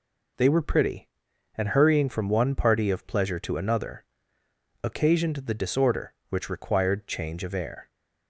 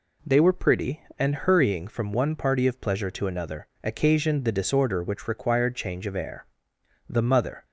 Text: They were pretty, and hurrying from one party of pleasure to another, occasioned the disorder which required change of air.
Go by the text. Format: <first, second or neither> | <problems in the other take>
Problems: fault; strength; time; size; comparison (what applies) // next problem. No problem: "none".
first | goes on to say "The mother"; from 7.0 s on; 0.56 s long